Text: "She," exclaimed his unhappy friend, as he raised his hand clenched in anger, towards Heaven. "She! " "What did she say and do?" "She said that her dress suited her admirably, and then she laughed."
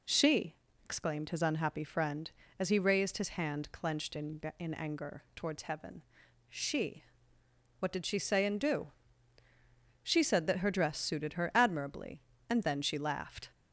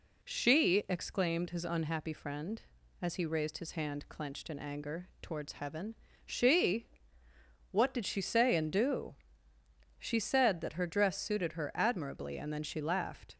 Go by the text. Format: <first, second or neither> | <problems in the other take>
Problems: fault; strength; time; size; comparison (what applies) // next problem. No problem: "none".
second | says "in" twice; at 4.5 s